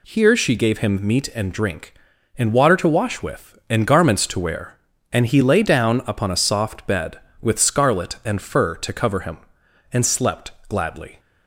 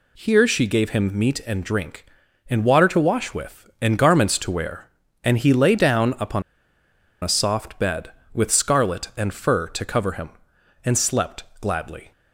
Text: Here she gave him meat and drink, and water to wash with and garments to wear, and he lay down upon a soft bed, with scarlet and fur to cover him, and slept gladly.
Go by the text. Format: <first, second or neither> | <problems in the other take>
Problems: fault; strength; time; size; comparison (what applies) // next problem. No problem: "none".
first | pauses between "upon" and "a"; noticeable; at 6.4 s; 0.79 s long // pauses between "slept" and "gladly"; slight; at 11.4 s; 0.16 s long; slight in the first